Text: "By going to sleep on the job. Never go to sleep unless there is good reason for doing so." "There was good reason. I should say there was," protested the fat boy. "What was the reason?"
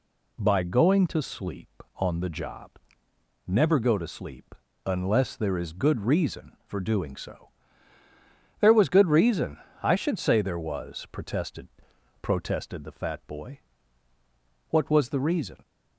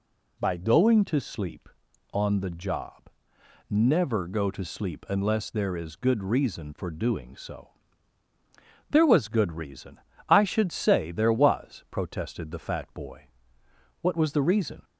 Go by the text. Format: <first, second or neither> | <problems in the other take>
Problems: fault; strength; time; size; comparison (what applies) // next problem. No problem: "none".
second | pauses between "sleep" and "unless"; slight; at 4.5 s; 0.30 s long // says "protested" twice; at 12.2 s